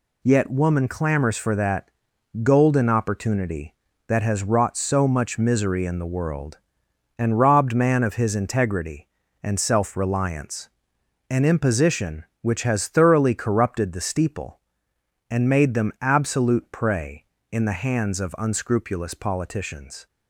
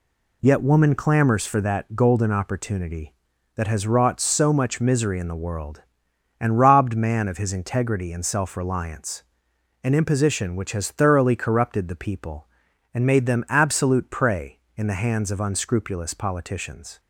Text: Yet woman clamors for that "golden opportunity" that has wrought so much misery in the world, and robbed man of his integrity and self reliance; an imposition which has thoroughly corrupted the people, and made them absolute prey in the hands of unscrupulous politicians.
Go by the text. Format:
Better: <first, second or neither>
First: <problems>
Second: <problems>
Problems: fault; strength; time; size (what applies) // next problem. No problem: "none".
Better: second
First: pauses between "that" and "golden"; noticeable; at 1.8 s; 0.54 s long // says "steeple" for "people"; at 13.9 s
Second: none